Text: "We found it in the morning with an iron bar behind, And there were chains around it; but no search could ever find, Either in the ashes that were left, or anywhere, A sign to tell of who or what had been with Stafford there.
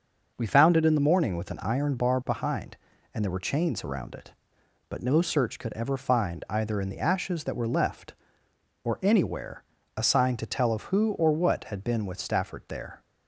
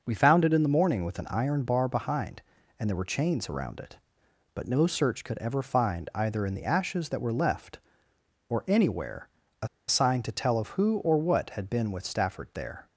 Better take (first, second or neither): first